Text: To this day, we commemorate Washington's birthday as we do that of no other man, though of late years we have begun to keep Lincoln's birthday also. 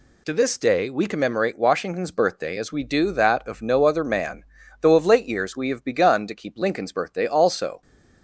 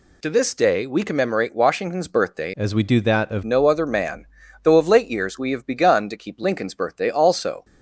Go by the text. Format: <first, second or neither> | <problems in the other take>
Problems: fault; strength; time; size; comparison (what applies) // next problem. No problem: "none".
first | changes voice from "as" to "of"; from 2.5 to 3.4 s; 0.9 s long